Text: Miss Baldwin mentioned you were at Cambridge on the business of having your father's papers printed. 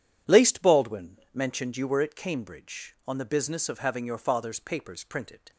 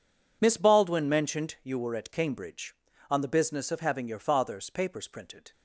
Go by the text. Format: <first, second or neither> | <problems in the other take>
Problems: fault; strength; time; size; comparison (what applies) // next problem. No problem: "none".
second | says "Laced" for "Miss"; at 0.2 s // pauses between "Baldwin" and "mentioned"; slight; at 1.1 s; 0.16 s long